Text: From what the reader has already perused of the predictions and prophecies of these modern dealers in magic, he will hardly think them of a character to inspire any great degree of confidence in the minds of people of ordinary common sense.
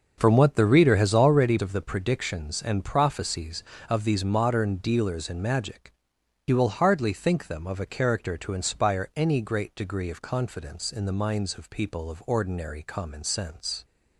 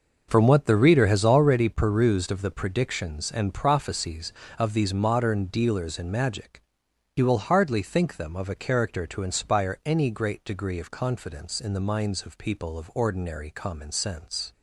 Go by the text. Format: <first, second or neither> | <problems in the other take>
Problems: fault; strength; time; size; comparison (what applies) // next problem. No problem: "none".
second | starts louder than the rest; until 1.1 s; 6 dB; noticeable in the second // skips "perused"; at 1.5 s